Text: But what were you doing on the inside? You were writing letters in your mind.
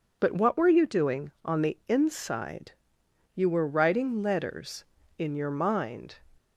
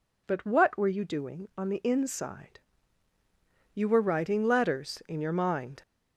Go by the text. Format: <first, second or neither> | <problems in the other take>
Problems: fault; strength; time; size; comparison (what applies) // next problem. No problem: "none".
first | gets louder; throughout; 3.5 dB